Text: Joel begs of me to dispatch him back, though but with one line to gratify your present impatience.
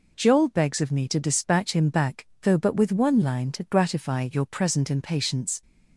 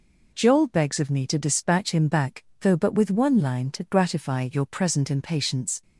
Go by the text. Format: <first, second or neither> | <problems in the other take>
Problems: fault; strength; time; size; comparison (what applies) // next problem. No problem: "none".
neither | none